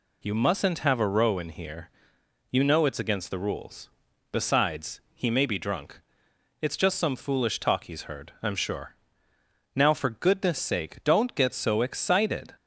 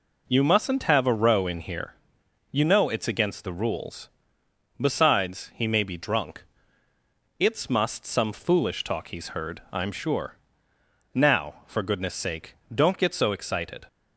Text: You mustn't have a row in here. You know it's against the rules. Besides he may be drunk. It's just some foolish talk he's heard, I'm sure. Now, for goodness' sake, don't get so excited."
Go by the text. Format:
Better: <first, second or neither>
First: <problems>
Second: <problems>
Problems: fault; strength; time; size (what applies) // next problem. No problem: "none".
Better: first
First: none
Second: says "must" for "just"; at 7.6 s